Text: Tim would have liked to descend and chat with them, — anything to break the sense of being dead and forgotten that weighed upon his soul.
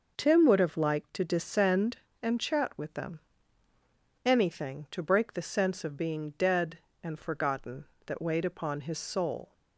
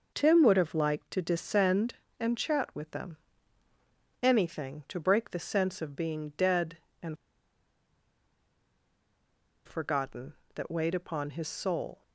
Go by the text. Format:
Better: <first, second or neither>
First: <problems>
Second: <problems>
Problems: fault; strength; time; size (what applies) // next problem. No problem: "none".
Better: first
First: none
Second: pauses between "and" and "forgotten"; strong; at 7.1 s; 2.5 s long